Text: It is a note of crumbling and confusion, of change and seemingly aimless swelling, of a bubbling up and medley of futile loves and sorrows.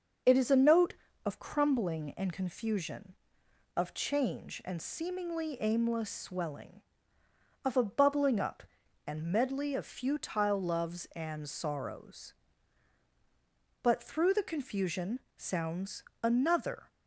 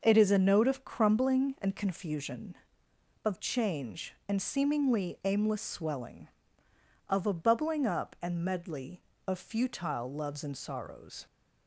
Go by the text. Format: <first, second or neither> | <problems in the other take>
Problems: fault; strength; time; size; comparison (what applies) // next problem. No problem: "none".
second | starts louder than the rest; noticeable; until 1.5 s; 6 dB; noticeable in the second // goes on to say "But through the confusion sounds another"; strong; from 13.8 s on; 3.0 s long